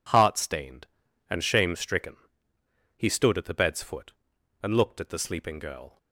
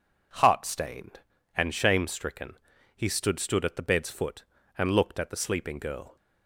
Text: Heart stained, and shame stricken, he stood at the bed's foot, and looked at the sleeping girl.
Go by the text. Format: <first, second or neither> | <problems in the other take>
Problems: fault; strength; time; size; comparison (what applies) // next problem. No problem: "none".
first | says "stood" twice; at 3.3 s